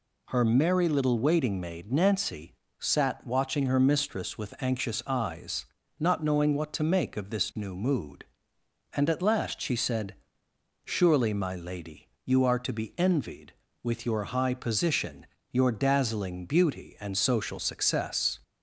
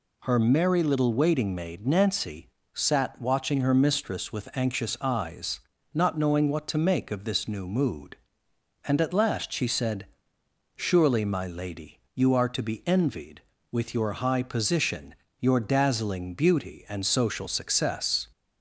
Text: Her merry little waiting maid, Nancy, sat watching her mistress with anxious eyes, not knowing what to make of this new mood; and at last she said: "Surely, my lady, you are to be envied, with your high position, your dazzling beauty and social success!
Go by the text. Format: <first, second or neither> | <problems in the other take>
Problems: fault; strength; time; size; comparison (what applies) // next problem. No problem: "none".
neither | none